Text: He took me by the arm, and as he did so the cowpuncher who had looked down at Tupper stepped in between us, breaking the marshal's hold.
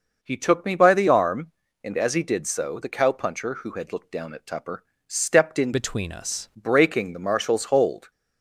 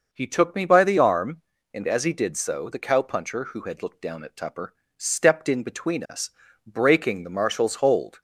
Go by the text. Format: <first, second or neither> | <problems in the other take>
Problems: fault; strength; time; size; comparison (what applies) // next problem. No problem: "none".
second | pauses between "Tupper" and "stepped"; slight; at 4.8 s; 0.24 s long; slight in the second // changes voice from "between" to "us"; from 5.7 to 6.4 s; 0.7 s long